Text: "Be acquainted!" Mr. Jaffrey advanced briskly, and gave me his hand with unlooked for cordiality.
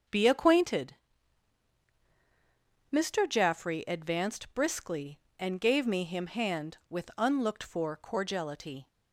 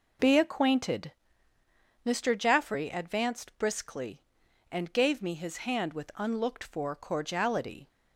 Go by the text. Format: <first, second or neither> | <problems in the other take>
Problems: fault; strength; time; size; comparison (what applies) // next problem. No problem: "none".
second | starts louder than the rest; until 3.0 s; 6.5 dB // says "him" for "his"; at 6.0 s